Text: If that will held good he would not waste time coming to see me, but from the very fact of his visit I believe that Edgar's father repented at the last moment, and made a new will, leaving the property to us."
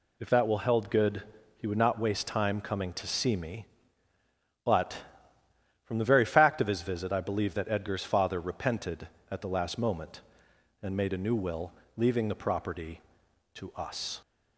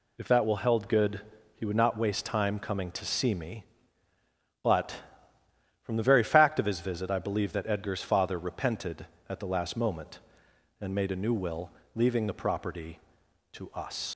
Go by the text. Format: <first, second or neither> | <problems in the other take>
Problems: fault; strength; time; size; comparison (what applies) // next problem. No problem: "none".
first | pauses between "good" and "he"; slight; at 1.2 s; 0.34 s long; slight in the first // leaves "us" unfinished; at 14.1 s; 55 ms